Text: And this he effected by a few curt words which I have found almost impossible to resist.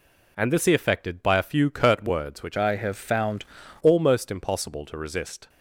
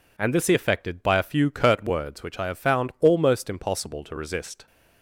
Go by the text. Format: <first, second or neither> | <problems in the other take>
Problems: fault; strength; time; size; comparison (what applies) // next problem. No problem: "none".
second | changes voice from "I" to "found"; from 2.5 to 3.4 s; 0.9 s long